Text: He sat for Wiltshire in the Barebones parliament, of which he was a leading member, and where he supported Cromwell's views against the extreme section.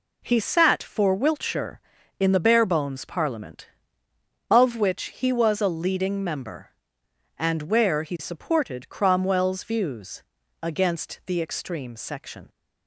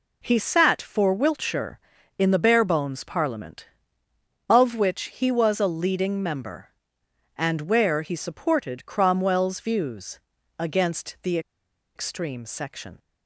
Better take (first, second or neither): first